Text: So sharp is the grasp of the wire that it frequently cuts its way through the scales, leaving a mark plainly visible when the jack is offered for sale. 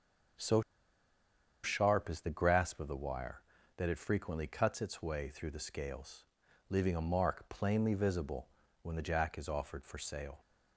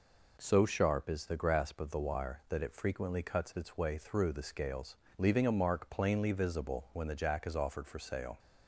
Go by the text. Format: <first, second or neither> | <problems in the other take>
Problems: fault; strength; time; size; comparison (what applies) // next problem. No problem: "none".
second | pauses between "So" and "sharp"; at 0.6 s; 1.0 s long // pauses between "visible" and "when"; slight; at 8.4 s; 0.34 s long